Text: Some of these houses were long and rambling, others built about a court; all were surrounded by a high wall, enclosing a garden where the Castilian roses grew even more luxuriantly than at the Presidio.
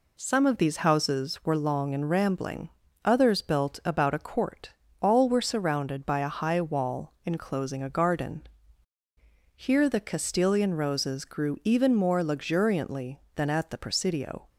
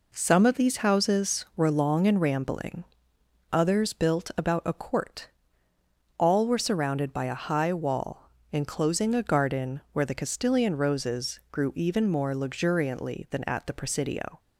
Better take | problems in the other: second | says "here" for "where"; at 9.5 s

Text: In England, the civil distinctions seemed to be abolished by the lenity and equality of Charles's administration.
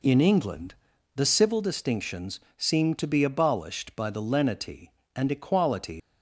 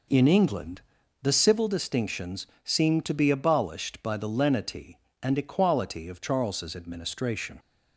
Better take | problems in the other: second | pauses between "distinctions" and "seemed"; slight; at 2.4 s; 0.16 s long; slight in the second // stops before "of Charles's administration"; at 5.9 s

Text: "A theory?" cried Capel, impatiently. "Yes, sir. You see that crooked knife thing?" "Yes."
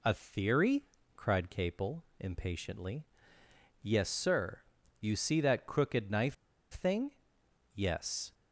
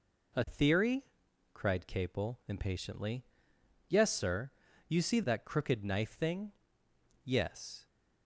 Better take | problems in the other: second | pauses between "knife" and "thing"; at 6.3 s; 0.38 s long

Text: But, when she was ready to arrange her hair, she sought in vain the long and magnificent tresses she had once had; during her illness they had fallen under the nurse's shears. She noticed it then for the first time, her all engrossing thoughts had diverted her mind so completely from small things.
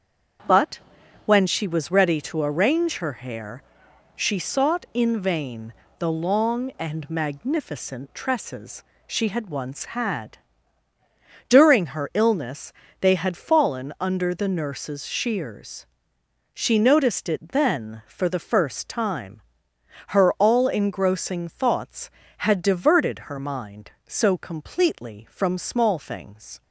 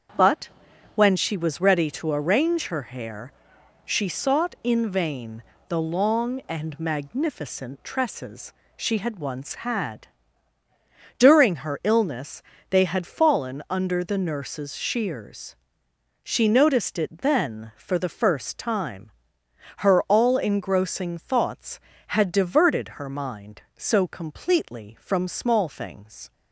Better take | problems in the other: neither | starts louder than the rest; the same in both // pauses between "vain" and "the"; slight; the same in both // pauses between "tresses" and "she"; slight; the same in both // pauses between "illness" and "they"; slight; the same in both

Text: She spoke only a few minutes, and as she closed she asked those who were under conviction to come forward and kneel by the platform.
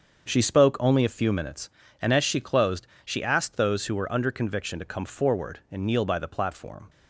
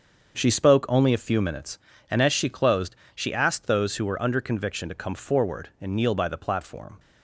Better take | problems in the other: neither | starts louder than the rest; the same in both // pauses between "closed" and "she"; slight; the same in both

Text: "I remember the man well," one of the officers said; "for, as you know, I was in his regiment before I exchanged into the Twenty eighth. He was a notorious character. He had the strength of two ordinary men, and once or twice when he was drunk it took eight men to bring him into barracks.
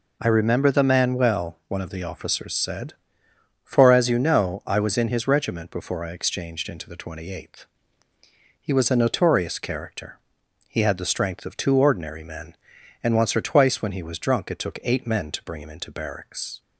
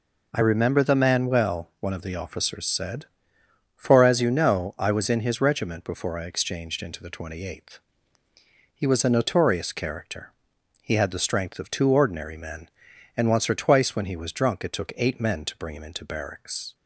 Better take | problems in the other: neither | none

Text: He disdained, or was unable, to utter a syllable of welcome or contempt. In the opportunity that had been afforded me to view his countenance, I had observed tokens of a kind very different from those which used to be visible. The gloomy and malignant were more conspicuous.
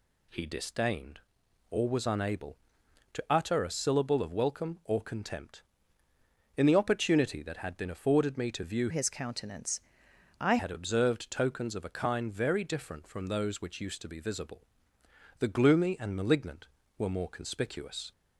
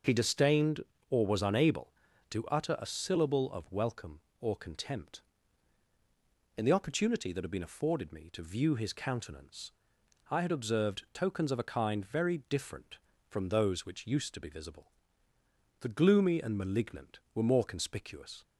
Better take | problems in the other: second | changes voice from "his" to "I"; from 8.8 to 10.5 s; 1.7 s long

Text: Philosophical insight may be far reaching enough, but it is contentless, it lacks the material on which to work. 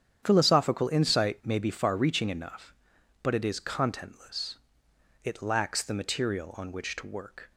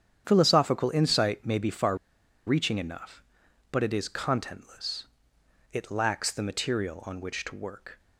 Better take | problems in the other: first | starts louder than the rest; strong; until 1.2 s; 8.5 dB; strong in the first // pauses between "far" and "reaching"; noticeable; at 1.9 s; 0.51 s long

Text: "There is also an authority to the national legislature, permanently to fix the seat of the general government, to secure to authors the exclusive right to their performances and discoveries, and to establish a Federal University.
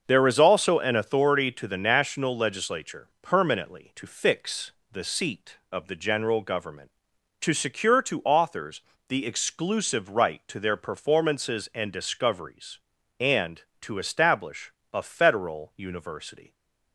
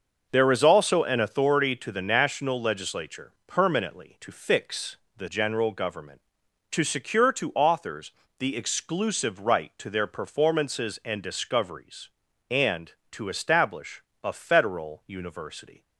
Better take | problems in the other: first | starts louder than the rest; noticeable; until 1.3 s; 6 dB; also in the first // pauses between "fix" and "the"; slight; at 4.9 s; 0.20 s long; slight in the first // skips "seat of the"; at 5.2 s // pauses between "authors" and "the"; slight; at 8.1 s; 0.26 s long; slight in the first // pauses between "establish" and "a"; slight; at 14.0 s; 0.22 s long; slight in the first

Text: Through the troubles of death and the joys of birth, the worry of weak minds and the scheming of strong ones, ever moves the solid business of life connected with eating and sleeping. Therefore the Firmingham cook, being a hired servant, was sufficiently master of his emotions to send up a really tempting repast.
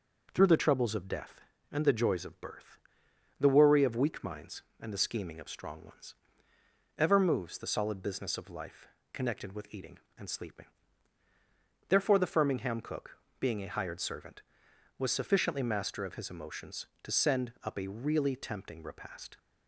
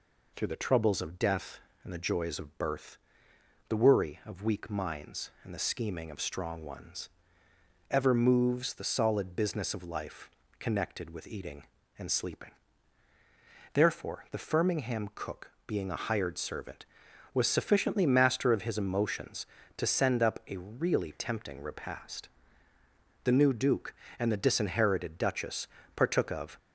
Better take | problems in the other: first | pauses between "life" and "connected"; slight; at 10.2 s; 0.28 s long; slight in the first // goes on to say "The new Duke and the disinherited Duchess partook of"; strong; from 23.2 s on; 3.3 s long

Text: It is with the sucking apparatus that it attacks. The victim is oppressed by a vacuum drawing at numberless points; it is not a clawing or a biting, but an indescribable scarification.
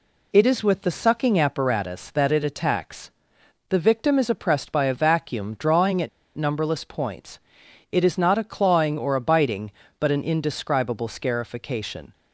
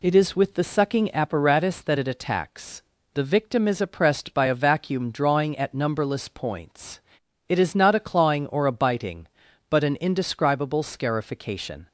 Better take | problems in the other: second | pauses between "at" and "numberless"; slight; at 6.0 s; 0.28 s long

